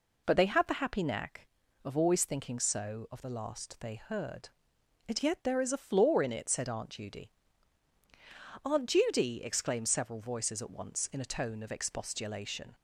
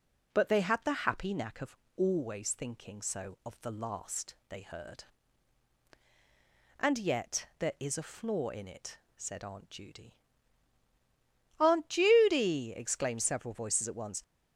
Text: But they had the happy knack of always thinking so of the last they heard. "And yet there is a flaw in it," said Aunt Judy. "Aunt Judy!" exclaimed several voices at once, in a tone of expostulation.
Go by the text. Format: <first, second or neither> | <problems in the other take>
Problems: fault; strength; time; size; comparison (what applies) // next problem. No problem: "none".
first | pauses between "of" and "always"; slight; at 1.7 s; 0.20 s long // stops before "in a tone of expostulation"; at 14.2 s